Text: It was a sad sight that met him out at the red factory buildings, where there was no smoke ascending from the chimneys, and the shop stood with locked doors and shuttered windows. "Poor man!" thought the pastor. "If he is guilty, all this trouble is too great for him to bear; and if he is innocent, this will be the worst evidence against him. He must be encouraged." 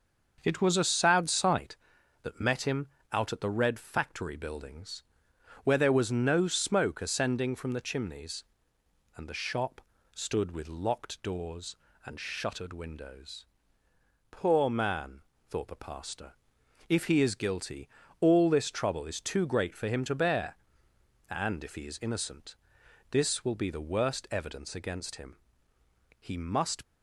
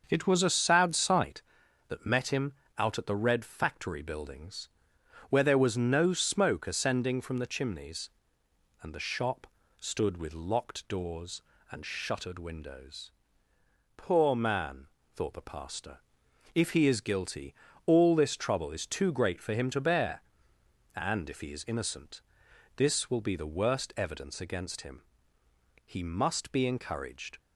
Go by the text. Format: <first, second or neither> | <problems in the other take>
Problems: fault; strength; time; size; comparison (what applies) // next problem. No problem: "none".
second | starts louder than the rest; until 1.4 s; 6.5 dB; also in the second // pauses between "him" and "out"; slight; at 2.8 s; 0.24 s long; slight in the second // pauses between "shop" and "stood"; slight; at 9.8 s; 0.34 s long; slight in the second // stops before "be encouraged"; at 26.8 s